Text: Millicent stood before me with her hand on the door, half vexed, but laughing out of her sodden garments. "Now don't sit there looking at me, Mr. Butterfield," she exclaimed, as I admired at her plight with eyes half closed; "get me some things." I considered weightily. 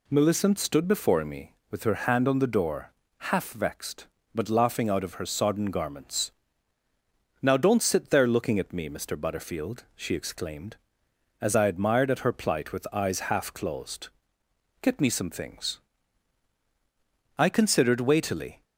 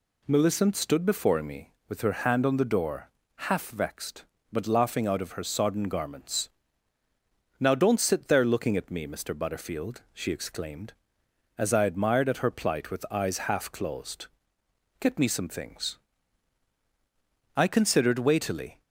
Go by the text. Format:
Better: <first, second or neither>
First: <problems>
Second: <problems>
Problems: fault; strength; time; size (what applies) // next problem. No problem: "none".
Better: neither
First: none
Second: none